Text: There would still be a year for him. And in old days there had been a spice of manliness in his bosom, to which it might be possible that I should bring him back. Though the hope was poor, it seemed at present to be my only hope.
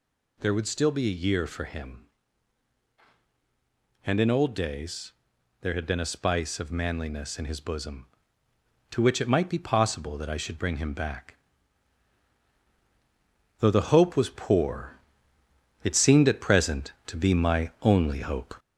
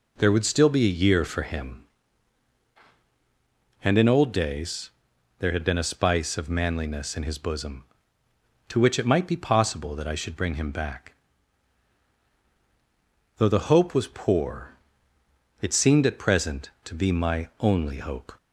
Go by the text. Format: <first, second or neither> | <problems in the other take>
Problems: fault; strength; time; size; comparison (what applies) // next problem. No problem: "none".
second | gets louder; slight; throughout; 3 dB // pauses between "days" and "there"; noticeable; at 5.1 s; 0.48 s long; noticeable in the second